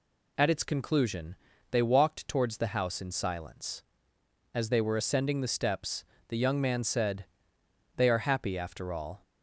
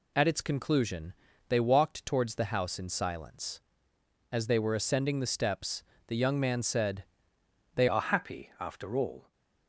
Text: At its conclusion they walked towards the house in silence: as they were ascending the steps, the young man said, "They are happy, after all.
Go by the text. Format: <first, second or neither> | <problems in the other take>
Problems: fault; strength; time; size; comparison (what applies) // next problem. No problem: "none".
first | pauses between "conclusion" and "they"; slight; at 1.1 s; 0.34 s long; slight in the first // changes voice at "are"; from 7.8 s on; 1.5 s long